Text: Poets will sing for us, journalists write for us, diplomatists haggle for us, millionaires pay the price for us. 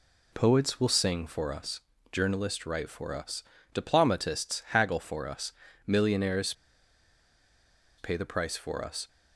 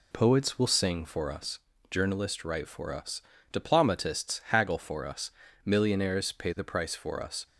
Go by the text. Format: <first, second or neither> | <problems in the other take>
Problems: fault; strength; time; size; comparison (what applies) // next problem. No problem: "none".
second | pauses between "millionaires" and "pay"; strong; at 6.5 s; 1.4 s long